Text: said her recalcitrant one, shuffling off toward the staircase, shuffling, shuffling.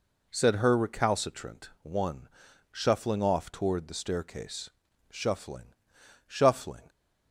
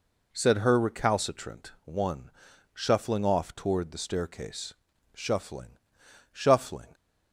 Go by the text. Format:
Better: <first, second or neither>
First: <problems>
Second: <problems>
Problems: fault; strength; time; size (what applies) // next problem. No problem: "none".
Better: neither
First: none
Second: none